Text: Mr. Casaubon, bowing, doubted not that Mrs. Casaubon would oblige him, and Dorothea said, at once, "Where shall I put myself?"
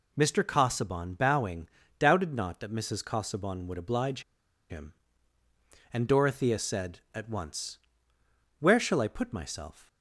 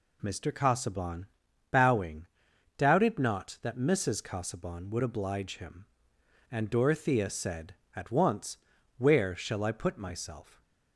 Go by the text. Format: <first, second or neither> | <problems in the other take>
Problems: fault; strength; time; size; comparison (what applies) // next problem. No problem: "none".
second | pauses between "oblige" and "him"; noticeable; at 4.2 s; 0.49 s long